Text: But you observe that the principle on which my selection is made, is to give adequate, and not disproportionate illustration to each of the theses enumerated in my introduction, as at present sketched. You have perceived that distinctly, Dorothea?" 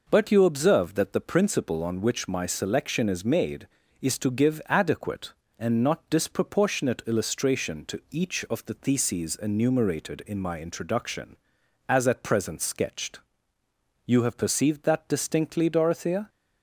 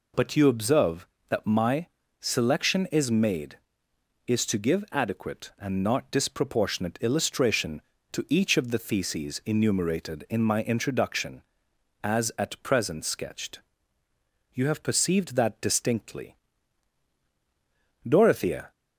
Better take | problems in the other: first | skips "the principle on which"; at 1.4 s // pauses between "my" and "selection"; slight; at 1.8 s; 0.34 s long

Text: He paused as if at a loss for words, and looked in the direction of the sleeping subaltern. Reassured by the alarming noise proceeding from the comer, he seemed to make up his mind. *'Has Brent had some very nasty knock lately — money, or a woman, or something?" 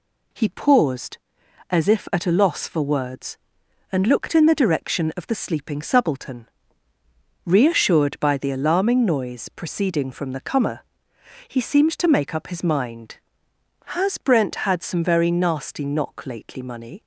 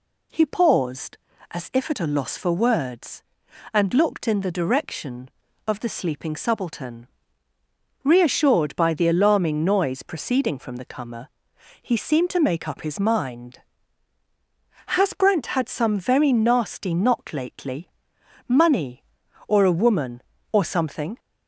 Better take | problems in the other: second | stops before "or a woman or something"; at 17.0 s

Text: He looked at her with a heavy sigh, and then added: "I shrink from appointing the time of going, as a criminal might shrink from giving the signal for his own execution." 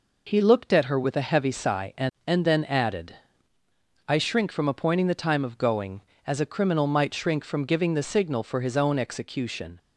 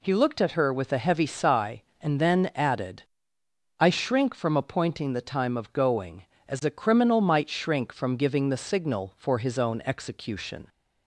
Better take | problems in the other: second | says "and" twice; at 2.2 s

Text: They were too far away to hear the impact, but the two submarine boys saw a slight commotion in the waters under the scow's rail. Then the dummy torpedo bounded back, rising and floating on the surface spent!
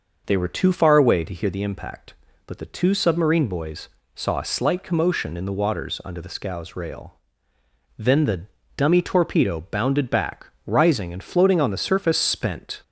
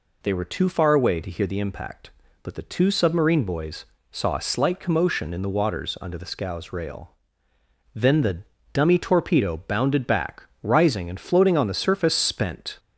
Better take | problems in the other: second | starts louder than the rest; noticeable; until 1.5 s; 5.5 dB // pauses between "boys" and "saw"; slight; at 3.8 s; 0.26 s long; slight in the second // pauses between "the" and "dummy"; slight; at 8.4 s; 0.34 s long; slight in the second

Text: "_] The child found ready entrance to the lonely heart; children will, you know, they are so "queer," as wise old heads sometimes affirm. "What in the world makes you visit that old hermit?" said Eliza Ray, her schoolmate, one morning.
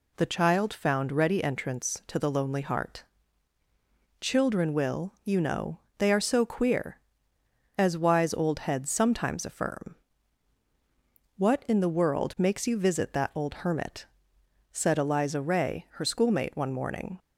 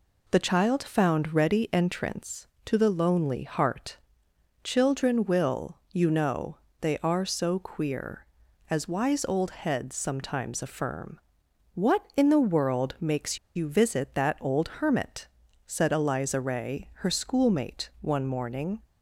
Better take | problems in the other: first | pauses between "makes" and "you"; slight; at 13.3 s; 0.17 s long

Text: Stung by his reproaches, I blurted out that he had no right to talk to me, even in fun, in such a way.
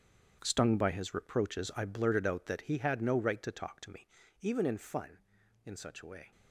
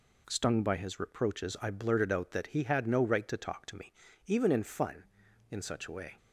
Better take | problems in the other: second | gets quieter; strong; throughout; 12.5 dB

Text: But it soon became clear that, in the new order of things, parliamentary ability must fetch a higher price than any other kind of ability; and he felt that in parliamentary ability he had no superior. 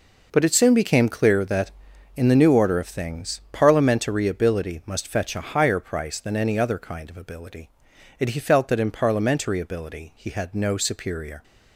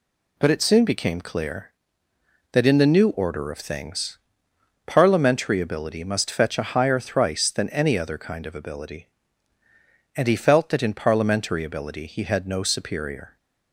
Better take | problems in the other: first | says "thrice" for "price"; at 6.9 s

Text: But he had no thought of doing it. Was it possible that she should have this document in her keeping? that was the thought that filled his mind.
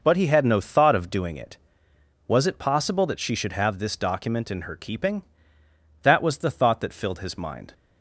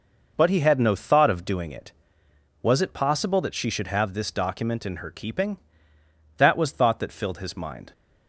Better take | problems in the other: first | skips "the"; at 6.7 s

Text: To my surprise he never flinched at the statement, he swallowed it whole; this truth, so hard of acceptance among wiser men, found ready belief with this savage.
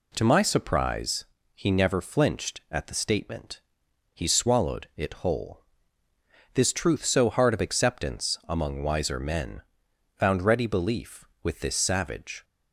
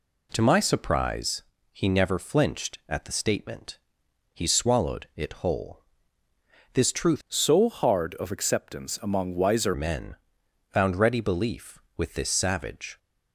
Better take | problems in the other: first | pauses between "surprise" and "he"; slight; at 1.4 s; 0.30 s long; slight in the first // changes voice from "so" to "wiser"; from 7.2 to 9.7 s; 2.5 s long

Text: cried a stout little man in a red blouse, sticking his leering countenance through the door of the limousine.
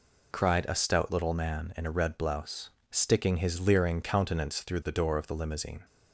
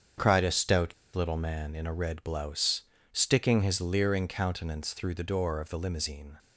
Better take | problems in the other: first | starts louder than the rest; strong; until 1.4 s; 7.5 dB // pauses between "stout" and "little"; slight; at 0.9 s; 0.22 s long

